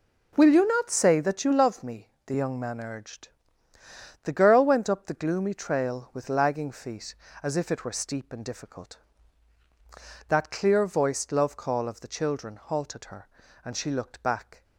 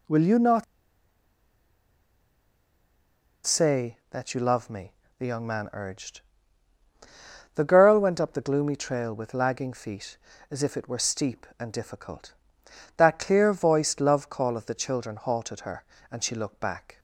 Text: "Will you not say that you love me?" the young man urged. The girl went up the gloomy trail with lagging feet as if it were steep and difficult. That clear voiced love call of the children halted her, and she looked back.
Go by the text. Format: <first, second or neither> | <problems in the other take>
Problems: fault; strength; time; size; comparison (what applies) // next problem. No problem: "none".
first | pauses between "not" and "say"; strong; at 0.6 s; 2.8 s long